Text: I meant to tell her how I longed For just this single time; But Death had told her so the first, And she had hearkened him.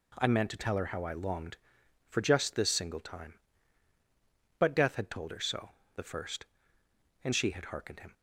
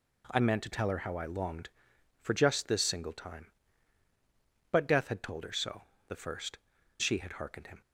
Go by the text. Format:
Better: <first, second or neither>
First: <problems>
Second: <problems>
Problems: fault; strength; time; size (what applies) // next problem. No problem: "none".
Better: first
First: pauses between "so" and "the"; slight; at 5.7 s; 0.24 s long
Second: pauses between "so" and "the"; slight; at 5.8 s; 0.24 s long // skips "And"; at 6.7 s